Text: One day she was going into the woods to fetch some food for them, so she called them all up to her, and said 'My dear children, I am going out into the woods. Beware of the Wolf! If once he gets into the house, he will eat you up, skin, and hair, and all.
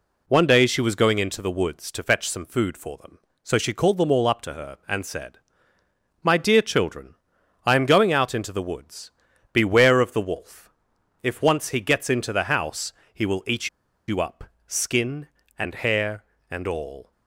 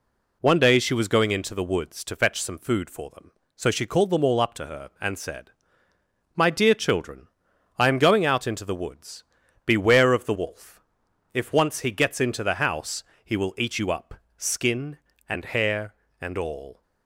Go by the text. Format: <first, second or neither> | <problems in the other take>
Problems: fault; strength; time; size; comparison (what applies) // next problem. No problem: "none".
second | pauses between "said" and "My"; noticeable; at 5.3 s; 0.84 s long; noticeable in the second // pauses between "eat" and "you"; at 13.6 s; 0.40 s long